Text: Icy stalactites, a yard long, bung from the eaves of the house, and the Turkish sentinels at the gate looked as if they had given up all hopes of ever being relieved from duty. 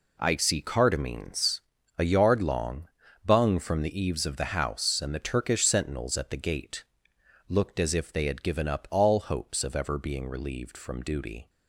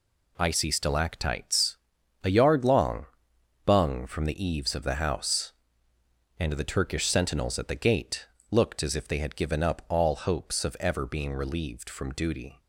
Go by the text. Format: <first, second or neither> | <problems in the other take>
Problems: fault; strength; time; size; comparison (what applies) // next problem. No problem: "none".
second | says "cardamines" for "stalactites"; at 0.6 s // pauses between "gate" and "looked"; noticeable; at 6.8 s; 0.64 s long; slight in the second